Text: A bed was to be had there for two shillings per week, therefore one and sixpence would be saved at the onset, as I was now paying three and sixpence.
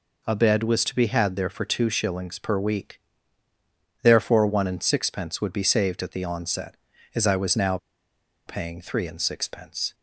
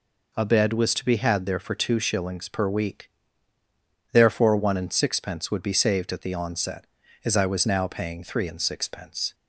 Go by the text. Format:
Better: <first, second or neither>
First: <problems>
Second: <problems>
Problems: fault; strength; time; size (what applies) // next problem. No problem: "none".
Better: second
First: pauses between "now" and "paying"; noticeable; at 7.7 s; 0.70 s long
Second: none